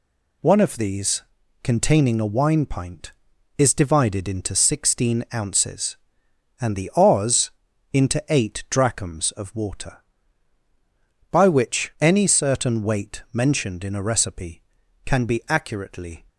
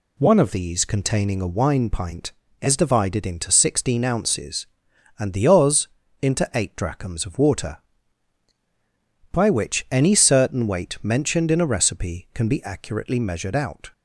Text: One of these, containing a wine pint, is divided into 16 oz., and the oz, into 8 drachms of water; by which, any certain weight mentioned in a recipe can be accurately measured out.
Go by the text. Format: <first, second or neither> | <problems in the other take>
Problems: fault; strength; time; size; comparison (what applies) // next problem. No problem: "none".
second | stops before "measured out"; at 16.2 s